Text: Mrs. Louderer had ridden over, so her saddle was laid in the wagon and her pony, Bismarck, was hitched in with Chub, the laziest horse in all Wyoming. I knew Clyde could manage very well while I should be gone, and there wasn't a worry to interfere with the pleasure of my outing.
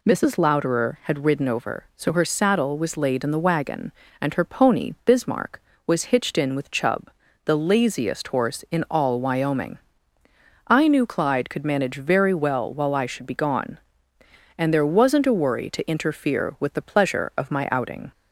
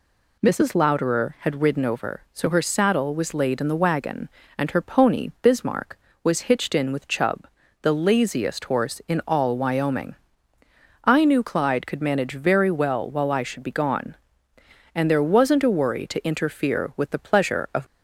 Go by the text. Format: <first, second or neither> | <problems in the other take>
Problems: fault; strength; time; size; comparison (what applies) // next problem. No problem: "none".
first | stops before "my outing"; at 17.8 s